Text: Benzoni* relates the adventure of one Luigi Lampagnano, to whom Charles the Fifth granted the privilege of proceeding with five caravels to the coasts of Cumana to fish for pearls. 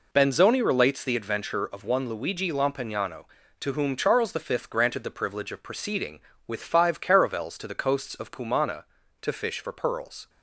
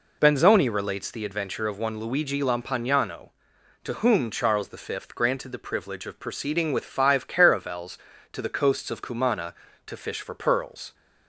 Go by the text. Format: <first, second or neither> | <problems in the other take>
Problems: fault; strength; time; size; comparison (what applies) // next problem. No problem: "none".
neither | none